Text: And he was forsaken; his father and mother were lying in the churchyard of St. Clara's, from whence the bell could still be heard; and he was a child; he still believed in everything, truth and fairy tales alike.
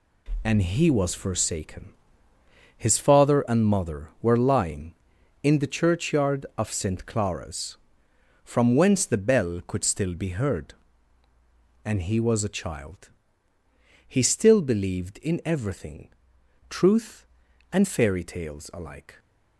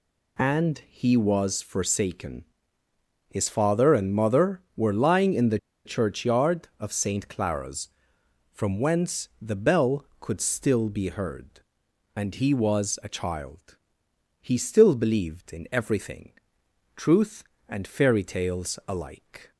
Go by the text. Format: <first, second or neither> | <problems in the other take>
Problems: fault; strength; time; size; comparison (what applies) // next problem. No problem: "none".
first | pauses between "the" and "churchyard"; slight; at 5.5 s; 0.27 s long